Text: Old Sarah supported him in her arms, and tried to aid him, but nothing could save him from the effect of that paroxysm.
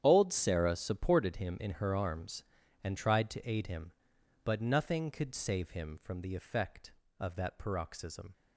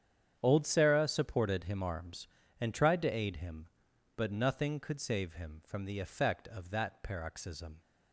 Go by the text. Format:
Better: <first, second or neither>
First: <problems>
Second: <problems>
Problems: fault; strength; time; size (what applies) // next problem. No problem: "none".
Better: first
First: starts louder than the rest; strong; until 1.0 s; 9.5 dB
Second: starts louder than the rest; strong; until 1.4 s; 8.5 dB // skips "in her"; at 1.8 s